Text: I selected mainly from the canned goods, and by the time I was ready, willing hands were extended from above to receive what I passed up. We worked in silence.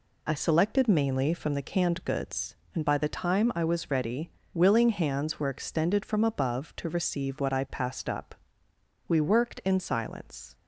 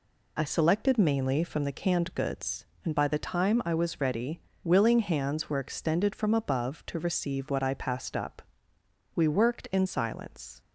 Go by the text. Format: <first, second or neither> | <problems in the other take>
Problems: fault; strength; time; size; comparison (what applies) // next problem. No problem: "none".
neither | none